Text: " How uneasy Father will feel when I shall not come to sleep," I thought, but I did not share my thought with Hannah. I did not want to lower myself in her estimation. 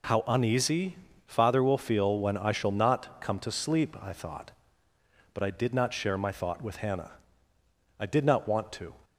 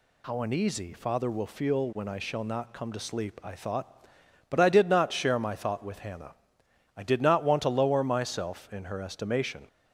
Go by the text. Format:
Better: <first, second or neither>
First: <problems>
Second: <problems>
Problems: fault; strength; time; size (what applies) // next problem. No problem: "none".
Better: second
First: pauses between "uneasy" and "Father"; slight; at 0.9 s; 0.28 s long // stops before "lower myself in her estimation"; at 9.0 s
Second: none